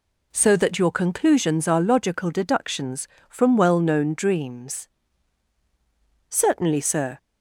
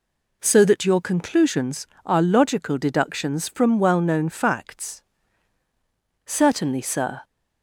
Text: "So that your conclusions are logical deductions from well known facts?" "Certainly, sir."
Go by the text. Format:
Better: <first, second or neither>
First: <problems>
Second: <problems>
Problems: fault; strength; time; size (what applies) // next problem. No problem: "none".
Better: second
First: says "dreams" for "facts"; at 4.1 s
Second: none